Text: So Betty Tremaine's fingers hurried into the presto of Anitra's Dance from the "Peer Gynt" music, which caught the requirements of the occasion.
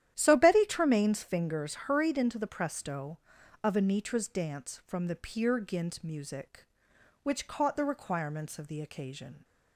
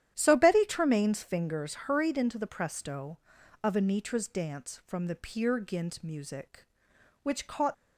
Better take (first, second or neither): first